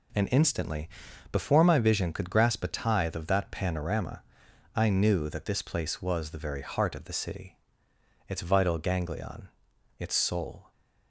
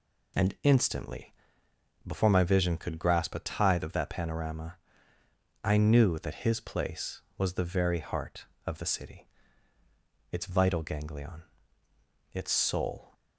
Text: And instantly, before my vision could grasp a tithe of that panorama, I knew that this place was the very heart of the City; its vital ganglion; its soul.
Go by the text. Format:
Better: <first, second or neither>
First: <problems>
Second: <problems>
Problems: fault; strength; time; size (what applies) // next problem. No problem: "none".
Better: first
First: none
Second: says "his" for "this"; at 6.4 s